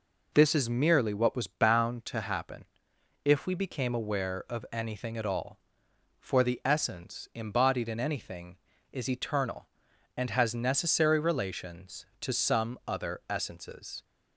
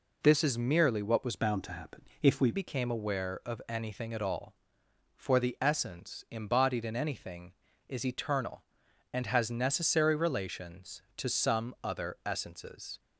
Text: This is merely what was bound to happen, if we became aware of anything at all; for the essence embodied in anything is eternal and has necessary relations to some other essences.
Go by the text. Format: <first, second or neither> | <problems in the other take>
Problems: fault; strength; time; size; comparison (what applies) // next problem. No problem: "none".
first | changes voice from "bound" to "we"; from 1.3 to 2.5 s; 1.2 s long